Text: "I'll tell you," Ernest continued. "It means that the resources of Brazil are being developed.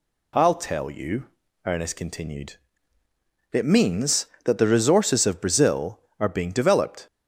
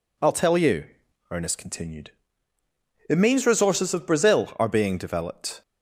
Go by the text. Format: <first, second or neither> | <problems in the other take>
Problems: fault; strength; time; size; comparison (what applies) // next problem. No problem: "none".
first | skips "that the"; at 3.4 s